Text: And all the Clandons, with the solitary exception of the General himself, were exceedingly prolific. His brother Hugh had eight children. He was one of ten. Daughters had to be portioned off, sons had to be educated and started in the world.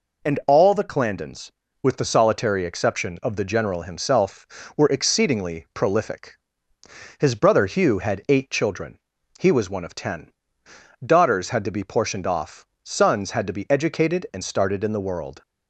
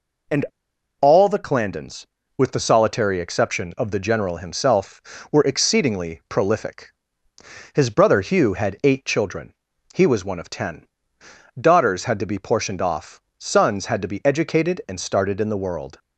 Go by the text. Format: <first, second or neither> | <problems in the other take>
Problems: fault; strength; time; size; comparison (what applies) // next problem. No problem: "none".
first | pauses between "And" and "all"; noticeable; at 0.4 s; 0.56 s long